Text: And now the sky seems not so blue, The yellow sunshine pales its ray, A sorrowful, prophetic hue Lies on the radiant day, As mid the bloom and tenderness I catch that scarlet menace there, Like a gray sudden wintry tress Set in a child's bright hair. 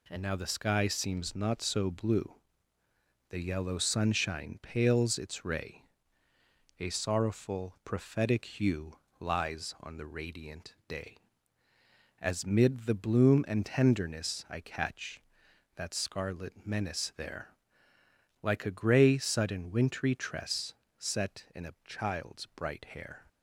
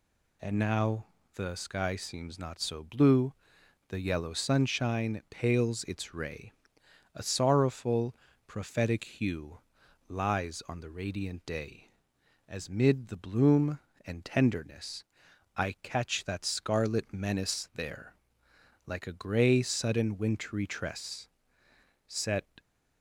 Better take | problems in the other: first | pauses between "now" and "the"; slight; at 1.0 s; 0.30 s long // pauses between "hue" and "Lies"; noticeable; at 9.5 s; 0.50 s long; slight in the first // pauses between "tenderness" and "I"; noticeable; at 15.0 s; 0.54 s long // pauses between "tress" and "Set"; noticeable; at 21.2 s; 0.80 s long; slight in the first // stops before "in a child's bright hair"; at 22.5 s

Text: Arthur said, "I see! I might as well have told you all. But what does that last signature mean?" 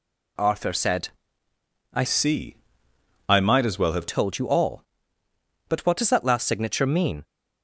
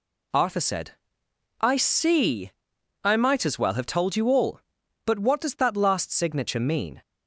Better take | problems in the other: second | changes voice from "see" to "have"; from 2.0 to 4.0 s; 2.0 s long

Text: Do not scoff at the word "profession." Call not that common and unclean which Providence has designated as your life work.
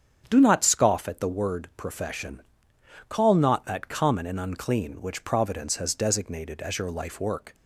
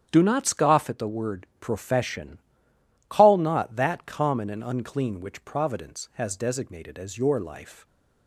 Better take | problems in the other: first | starts louder than the rest; strong; until 1.1 s; 9 dB; strong in the first // stops before "work"; at 7.8 s

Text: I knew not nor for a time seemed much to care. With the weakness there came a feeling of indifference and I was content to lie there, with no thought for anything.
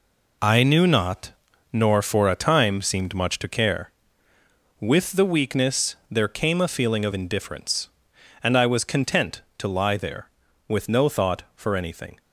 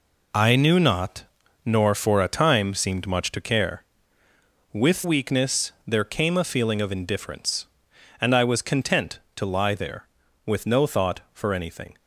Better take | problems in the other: first | pauses between "not" and "nor"; at 1.2 s; 0.40 s long; also in the first // skips "the"; at 5.0 s

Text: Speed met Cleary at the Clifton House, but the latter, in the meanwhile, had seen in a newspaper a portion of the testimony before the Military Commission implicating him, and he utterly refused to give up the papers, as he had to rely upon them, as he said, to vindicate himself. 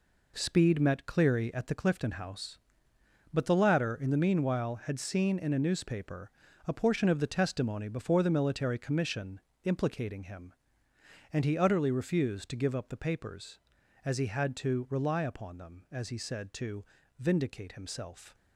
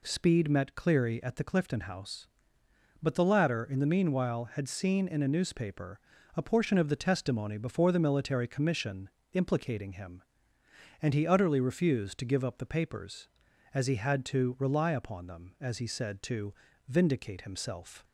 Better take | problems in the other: second | gets quieter; strong; throughout; 8.5 dB // pauses between "newspaper" and "a"; at 6.2 s; 0.38 s long; also in the second // pauses between "Commission" and "implicating"; slight; at 9.3 s; 0.24 s long; slight in the second // pauses between "to" and "vindicate"; slight; at 16.8 s; 0.34 s long; slight in the second

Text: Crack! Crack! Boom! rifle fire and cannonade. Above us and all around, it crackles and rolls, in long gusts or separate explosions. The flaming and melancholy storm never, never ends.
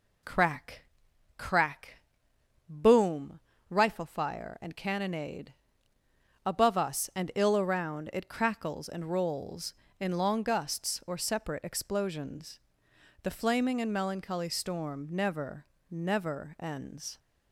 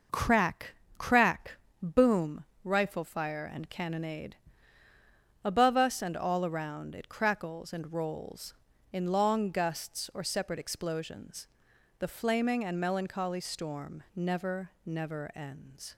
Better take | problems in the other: second | says "ill" for "all"; at 7.3 s

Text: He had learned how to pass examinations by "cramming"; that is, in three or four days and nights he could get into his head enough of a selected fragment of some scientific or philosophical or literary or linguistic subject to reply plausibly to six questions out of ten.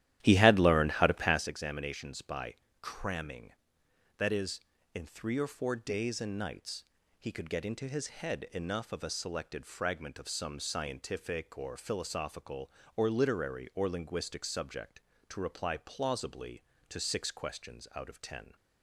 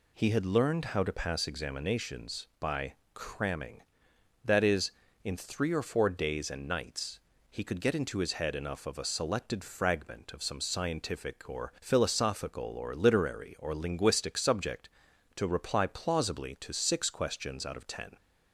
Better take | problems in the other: second | starts louder than the rest; strong; until 1.6 s; 13 dB // pauses between "by" and "cramming"; slight; at 2.5 s; 0.28 s long; slight in the second // pauses between "nights" and "he"; slight; at 6.8 s; 0.34 s long; slight in the second

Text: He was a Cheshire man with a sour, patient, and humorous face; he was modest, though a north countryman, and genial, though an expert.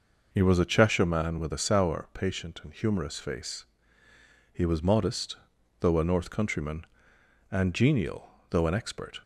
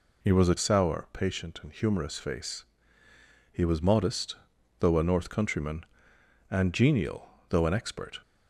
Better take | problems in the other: first | skips "Cheshire man with a"; at 0.5 s

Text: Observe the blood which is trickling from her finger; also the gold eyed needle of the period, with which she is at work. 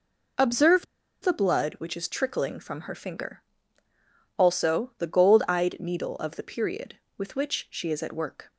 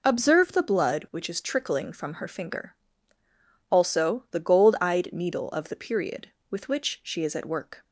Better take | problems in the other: second | pauses between "Observe" and "the"; at 0.8 s; 0.37 s long

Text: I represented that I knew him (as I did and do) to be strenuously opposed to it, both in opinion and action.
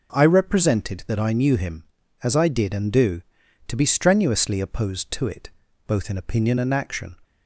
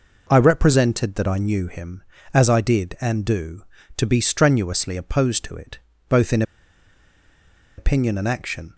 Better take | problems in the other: first | pauses between "in" and "opinion"; strong; at 6.4 s; 1.3 s long

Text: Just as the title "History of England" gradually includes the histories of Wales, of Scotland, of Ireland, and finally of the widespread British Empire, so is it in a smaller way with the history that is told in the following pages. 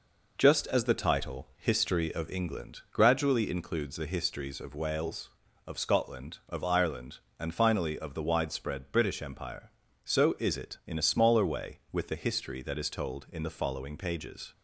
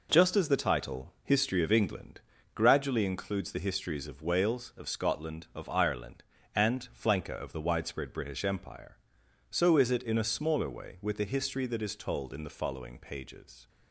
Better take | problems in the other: first | pauses between "England" and "gradually"; slight; at 2.1 s; 0.36 s long // says "flanker" for "finally"; at 6.9 s

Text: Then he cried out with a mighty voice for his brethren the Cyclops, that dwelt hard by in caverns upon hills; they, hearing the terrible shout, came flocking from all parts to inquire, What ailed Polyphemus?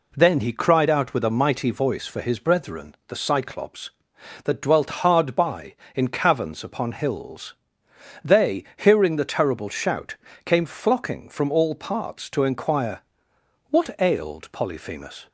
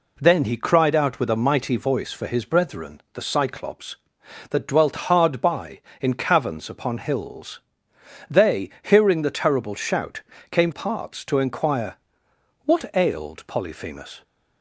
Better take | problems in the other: first | skips "flocking from all"; at 10.7 s

